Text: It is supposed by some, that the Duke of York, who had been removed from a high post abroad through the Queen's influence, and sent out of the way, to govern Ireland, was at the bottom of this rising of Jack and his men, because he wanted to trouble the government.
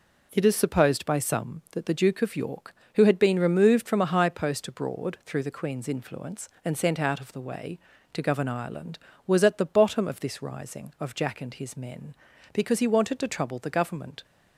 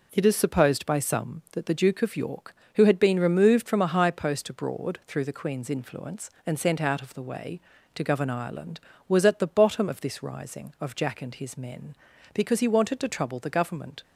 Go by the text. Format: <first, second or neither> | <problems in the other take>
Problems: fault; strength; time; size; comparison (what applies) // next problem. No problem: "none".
neither | none